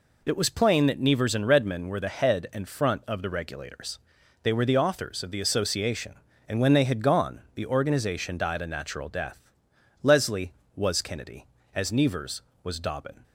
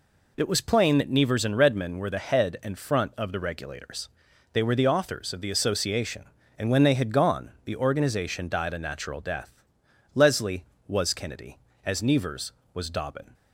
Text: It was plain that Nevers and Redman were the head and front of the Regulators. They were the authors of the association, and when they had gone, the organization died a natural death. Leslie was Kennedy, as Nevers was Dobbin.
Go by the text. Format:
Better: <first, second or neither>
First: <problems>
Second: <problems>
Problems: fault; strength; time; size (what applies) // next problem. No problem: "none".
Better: neither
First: none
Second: none